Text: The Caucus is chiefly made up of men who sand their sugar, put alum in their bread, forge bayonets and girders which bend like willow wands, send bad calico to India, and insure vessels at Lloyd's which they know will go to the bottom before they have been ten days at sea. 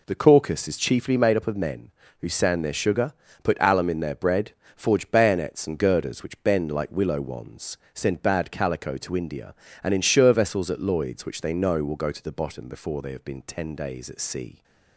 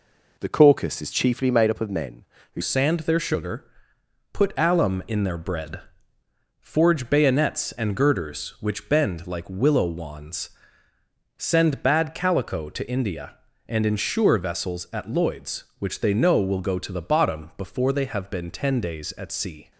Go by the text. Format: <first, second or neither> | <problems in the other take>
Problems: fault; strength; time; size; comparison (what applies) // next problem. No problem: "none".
first | changes voice at "sand"; from 2.6 s on; 17.1 s long